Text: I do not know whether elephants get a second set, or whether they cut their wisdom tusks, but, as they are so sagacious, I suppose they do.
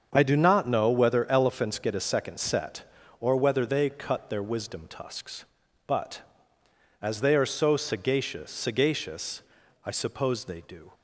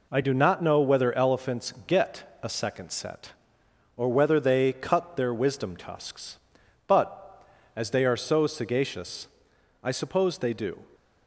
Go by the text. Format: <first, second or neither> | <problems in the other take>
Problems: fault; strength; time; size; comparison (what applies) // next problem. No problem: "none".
second | starts louder than the rest; until 1.1 s; 7 dB // says "sagacious" twice; at 8.4 s